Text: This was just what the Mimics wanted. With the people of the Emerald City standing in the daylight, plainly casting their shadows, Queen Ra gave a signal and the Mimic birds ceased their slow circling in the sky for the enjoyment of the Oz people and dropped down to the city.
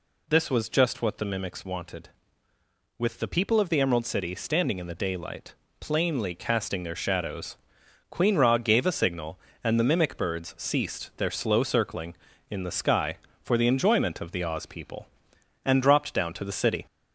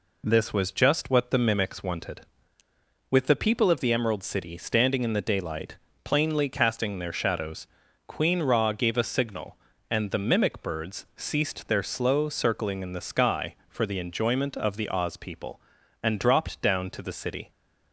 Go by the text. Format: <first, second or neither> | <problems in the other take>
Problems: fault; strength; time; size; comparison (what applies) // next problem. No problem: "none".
second | gets louder; slight; throughout; 2.5 dB